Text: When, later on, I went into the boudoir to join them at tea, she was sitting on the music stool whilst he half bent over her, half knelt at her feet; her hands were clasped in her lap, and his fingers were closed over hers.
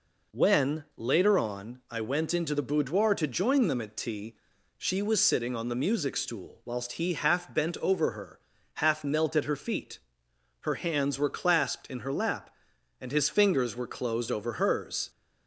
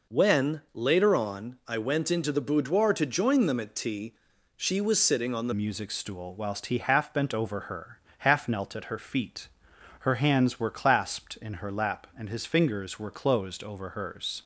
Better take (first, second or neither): first